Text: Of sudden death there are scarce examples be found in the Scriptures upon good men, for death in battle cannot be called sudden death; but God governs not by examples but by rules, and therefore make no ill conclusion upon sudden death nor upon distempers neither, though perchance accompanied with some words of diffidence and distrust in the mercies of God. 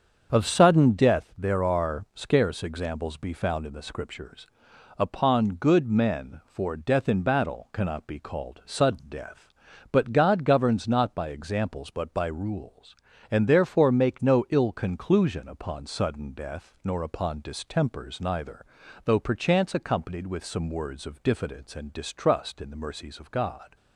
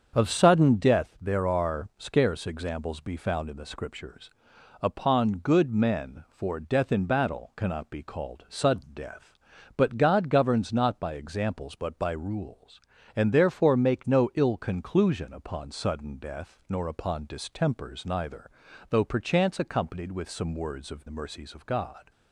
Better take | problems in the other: first | starts louder than the rest; until 1.1 s; 7 dB; also in the first // pauses between "Scriptures" and "upon"; noticeable; at 4.3 s; 0.50 s long; noticeable in the first // skips "diffidence and distrust in"; at 21.0 s

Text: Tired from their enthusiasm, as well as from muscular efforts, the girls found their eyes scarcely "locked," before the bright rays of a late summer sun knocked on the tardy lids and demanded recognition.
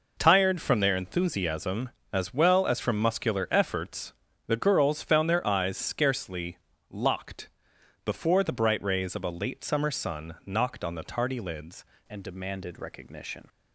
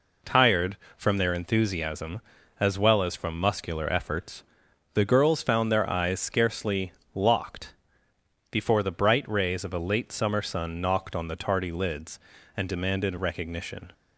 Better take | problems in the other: second | pauses between "scarcely" and "locked"; slight; at 6.5 s; 0.32 s long; slight in the second // changes voice at "and"; from 12.0 s on; 1.4 s long

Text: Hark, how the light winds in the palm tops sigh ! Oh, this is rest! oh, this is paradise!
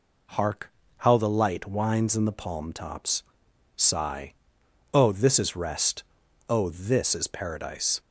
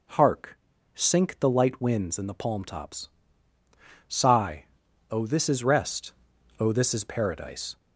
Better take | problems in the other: first | says "sink" for "how"; at 0.9 s // pauses between "tops" and "sigh"; at 3.0 s; 1.0 s long; noticeable in the first

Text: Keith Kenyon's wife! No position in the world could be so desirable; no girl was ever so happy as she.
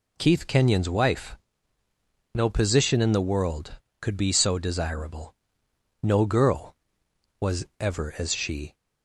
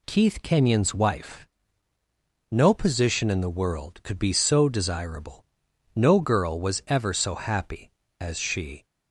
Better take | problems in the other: second | pauses between "was" and "ever"; slight; at 7.6 s; 0.16 s long // skips "so happy"; at 8.1 s

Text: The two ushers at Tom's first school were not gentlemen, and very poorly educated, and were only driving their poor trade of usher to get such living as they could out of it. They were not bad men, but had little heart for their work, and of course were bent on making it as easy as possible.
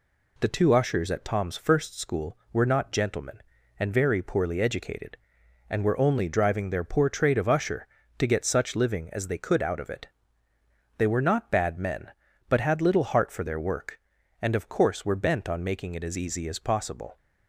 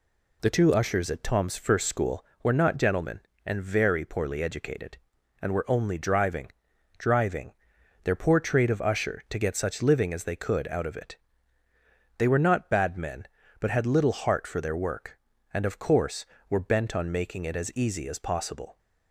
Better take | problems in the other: first | says "driving" twice; at 6.9 s

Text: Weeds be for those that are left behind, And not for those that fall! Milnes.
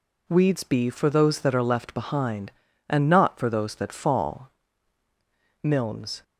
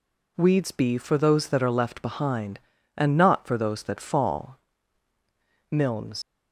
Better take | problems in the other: first | leaves "Milnes" unfinished; at 6.2 s; 85 ms

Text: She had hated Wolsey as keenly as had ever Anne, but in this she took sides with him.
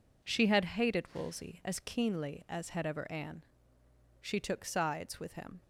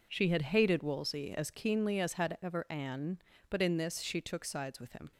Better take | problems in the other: second | skips "but in this"; at 3.8 s

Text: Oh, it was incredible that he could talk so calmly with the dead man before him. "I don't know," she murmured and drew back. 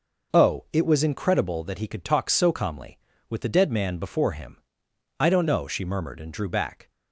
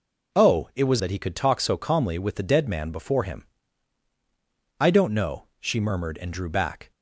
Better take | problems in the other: first | skips "incredible"; at 0.9 s

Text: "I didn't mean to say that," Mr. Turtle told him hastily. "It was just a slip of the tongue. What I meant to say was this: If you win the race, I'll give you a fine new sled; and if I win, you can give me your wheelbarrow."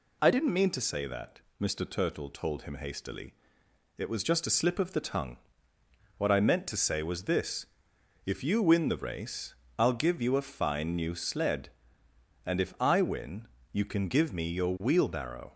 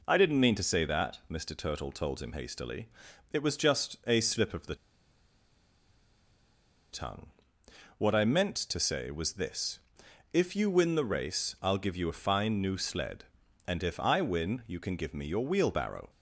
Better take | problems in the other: first | pauses between "the" and "tongue"; strong; at 4.7 s; 2.1 s long

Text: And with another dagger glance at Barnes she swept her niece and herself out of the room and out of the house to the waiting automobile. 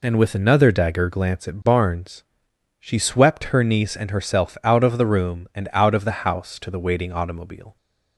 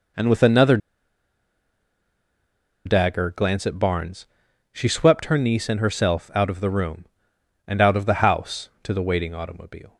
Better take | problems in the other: first | pauses between "another" and "dagger"; strong; at 0.7 s; 2.0 s long // pauses between "Barnes" and "she"; noticeable; at 4.2 s; 0.46 s long; noticeable in the first

